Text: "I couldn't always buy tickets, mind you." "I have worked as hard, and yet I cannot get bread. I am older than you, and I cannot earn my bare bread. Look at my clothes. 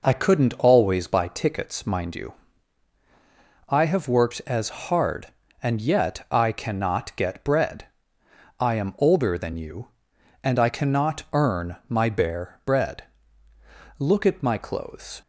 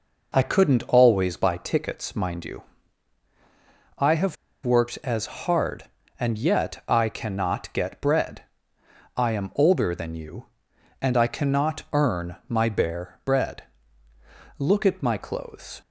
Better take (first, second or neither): first